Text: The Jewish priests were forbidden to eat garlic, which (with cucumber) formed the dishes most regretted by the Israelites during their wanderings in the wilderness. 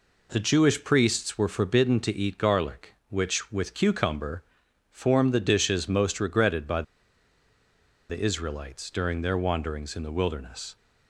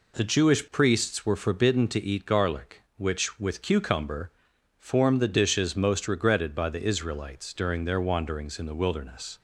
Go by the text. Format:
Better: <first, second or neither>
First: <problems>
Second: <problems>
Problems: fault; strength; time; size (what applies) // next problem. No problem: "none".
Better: second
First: pauses between "by" and "the"; strong; at 6.8 s; 1.2 s long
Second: none